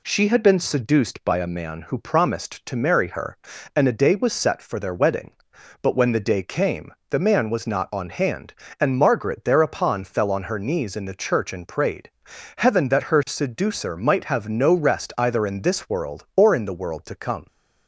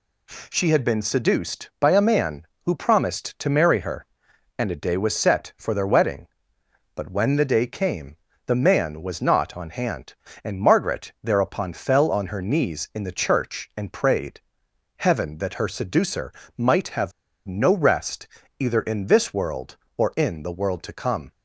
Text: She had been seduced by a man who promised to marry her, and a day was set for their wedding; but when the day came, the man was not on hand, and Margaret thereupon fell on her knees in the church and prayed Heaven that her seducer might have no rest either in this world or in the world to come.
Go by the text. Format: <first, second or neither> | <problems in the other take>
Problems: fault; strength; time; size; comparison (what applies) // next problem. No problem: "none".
first | pauses between "prayed" and "Heaven"; noticeable; at 14.4 s; 0.56 s long; noticeable in the first // pauses between "seducer" and "might"; slight; at 16.3 s; 0.24 s long // pauses between "have" and "no"; slight; at 17.1 s; 0.34 s long // pauses between "rest" and "either"; slight; at 18.2 s; 0.32 s long